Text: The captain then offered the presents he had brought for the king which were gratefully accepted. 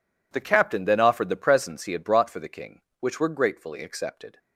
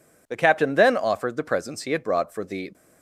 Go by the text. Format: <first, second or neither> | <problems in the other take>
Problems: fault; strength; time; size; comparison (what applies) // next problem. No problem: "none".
first | stops before "king which were gratefully accepted"; at 2.7 s